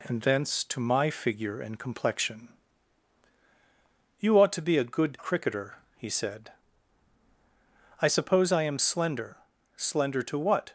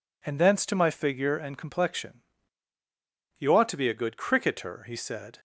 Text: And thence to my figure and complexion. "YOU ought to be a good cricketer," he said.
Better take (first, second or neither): second